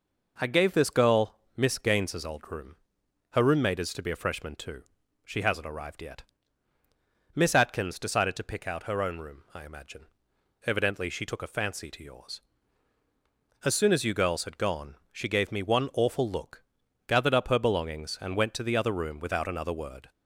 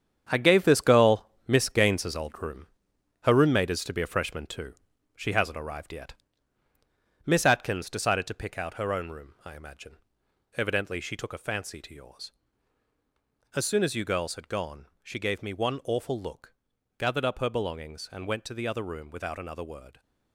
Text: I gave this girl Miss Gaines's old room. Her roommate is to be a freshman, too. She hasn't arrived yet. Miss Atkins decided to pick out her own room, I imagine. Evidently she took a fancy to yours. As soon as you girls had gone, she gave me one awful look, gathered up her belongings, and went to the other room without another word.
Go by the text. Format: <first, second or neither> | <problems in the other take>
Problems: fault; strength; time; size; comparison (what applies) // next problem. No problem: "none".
first | gets quieter; strong; throughout; 9 dB // pauses between "girl" and "Miss"; slight; at 1.2 s; 0.18 s long; slight in the first